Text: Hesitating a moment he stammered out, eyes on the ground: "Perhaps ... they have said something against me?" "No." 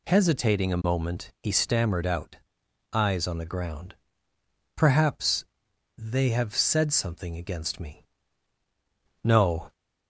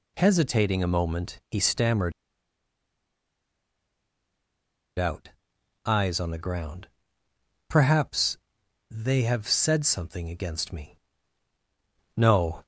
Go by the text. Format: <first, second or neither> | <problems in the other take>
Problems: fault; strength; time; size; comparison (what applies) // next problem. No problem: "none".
first | pauses between "stammered" and "out"; strong; at 2.1 s; 2.8 s long